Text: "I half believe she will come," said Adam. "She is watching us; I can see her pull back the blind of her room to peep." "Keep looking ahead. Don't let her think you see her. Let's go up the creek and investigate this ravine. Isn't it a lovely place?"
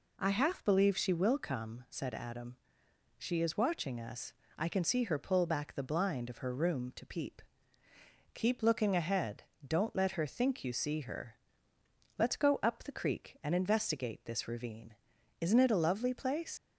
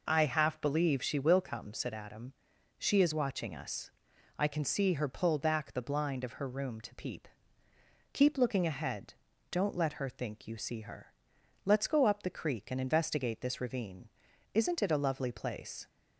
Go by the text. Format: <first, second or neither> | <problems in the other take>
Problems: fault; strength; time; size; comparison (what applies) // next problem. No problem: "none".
second | leaves "place" unfinished; at 16.5 s; 110 ms